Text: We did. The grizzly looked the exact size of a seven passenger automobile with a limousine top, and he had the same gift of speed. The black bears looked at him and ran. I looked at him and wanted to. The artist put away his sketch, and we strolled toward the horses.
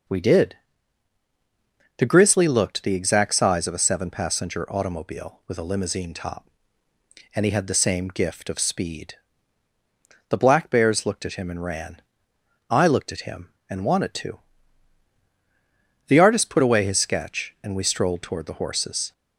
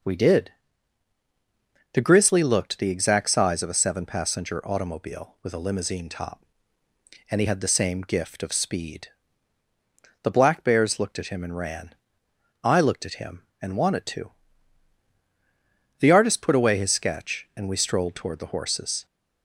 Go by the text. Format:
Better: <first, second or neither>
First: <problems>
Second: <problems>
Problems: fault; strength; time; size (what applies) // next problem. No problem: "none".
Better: neither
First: none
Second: none